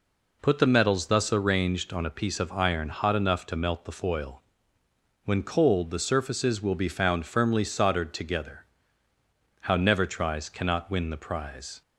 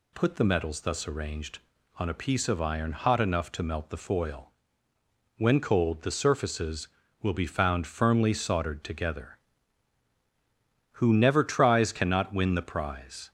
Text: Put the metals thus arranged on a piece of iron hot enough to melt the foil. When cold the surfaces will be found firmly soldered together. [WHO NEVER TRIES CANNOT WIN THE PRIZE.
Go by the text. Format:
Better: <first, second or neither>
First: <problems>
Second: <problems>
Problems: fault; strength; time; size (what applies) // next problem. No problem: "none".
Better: second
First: says "How" for "WHO"; at 9.6 s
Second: none